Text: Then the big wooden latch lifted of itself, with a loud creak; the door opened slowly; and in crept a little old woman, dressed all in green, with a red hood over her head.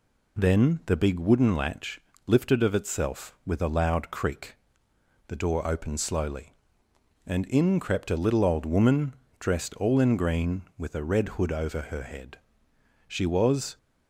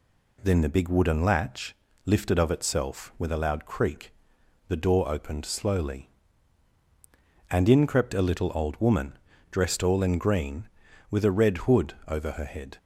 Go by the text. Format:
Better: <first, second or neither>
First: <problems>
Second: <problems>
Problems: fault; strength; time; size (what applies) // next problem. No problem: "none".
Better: second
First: pauses between "latch" and "lifted"; slight; at 1.9 s; 0.28 s long // goes on to say "She was"; noticeable; from 13.0 s on; 0.70 s long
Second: pauses between "latch" and "lifted"; slight; at 1.7 s; 0.30 s long